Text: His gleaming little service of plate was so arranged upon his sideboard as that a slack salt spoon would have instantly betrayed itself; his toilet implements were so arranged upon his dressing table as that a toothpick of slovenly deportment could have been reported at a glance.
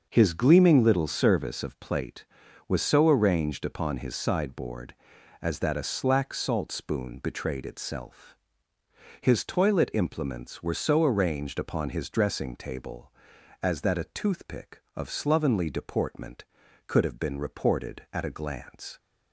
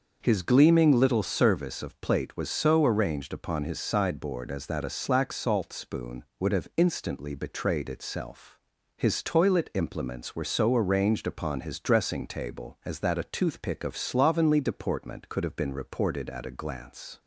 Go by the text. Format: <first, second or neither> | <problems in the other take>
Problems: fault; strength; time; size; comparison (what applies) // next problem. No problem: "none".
second | starts louder than the rest; until 1.1 s; 6 dB; noticeable in the second // skips "would have instantly"; at 7.1 s